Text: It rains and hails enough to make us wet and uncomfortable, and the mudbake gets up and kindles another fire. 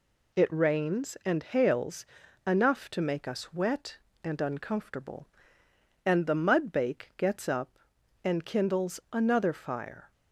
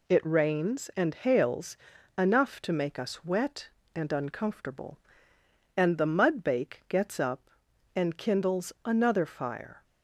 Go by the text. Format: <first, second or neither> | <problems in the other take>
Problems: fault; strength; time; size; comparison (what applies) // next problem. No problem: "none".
neither | pauses between "hails" and "enough"; the same in both